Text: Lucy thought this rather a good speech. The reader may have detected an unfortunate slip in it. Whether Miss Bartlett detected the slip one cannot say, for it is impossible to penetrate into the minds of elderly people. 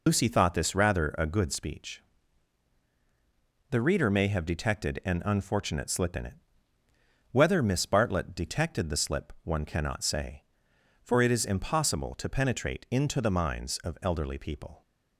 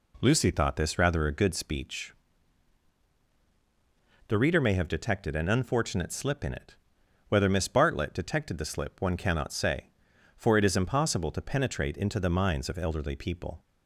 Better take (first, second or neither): second